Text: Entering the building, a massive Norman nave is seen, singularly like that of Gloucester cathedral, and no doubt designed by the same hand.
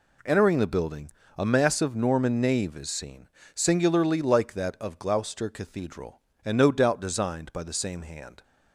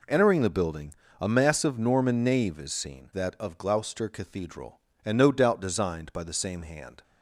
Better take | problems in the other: first | skips "singularly like"; at 3.1 s

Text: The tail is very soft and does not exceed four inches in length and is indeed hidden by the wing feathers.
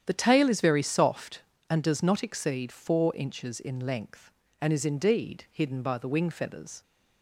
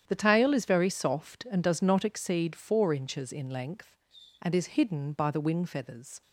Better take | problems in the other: first | starts louder than the rest; strong; until 1.0 s; 9.5 dB; strong in the first // skips "indeed"; at 4.7 s

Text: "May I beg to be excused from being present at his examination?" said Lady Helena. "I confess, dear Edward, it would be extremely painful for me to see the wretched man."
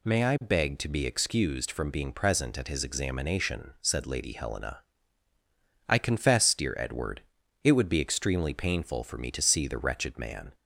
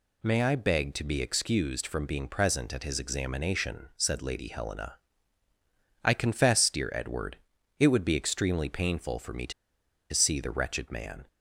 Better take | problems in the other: first | pauses between "to" and "see"; noticeable; at 9.5 s; 0.60 s long

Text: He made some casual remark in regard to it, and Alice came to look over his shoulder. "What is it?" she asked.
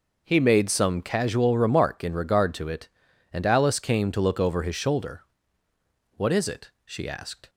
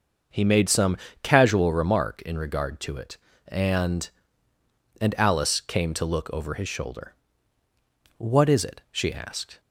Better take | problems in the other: first | starts louder than the rest; until 1.6 s; 6 dB // pauses between "some" and "casual"; slight; at 0.9 s; 0.26 s long // says "and" twice; at 4.9 s

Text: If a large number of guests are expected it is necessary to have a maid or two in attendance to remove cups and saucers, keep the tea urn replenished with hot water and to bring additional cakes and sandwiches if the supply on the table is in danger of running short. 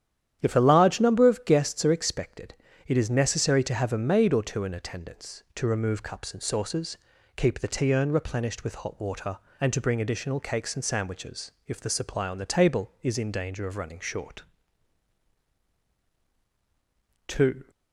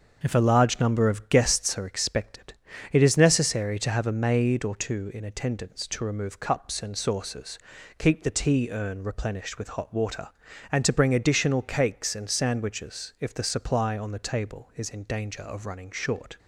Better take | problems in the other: second | starts louder than the rest; strong; until 1.4 s; 10 dB; also in the second // pauses between "expected" and "it"; slight; at 2.5 s; 0.32 s long; slight in the second // pauses between "sandwiches" and "if"; slight; at 11.5 s; 0.16 s long // goes on to say "Two"; slight; from 17.2 s on; 0.38 s long

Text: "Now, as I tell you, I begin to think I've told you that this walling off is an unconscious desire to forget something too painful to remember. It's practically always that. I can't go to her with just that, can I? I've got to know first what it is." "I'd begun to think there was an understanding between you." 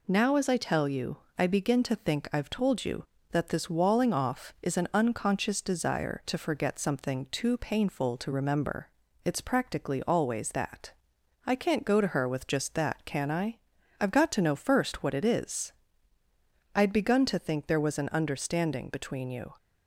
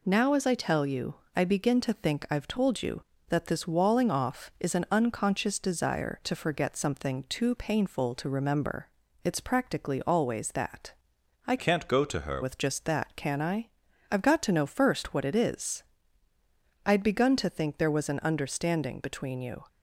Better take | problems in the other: first | changes voice from "can't" to "her"; from 11.5 to 12.4 s; 0.9 s long

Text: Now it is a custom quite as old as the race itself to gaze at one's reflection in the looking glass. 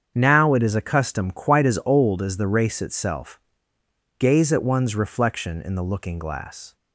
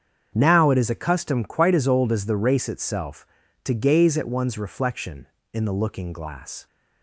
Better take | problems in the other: second | starts louder than the rest; strong; until 1.1 s; 7.5 dB; strong in the second // skips "to"; at 3.7 s

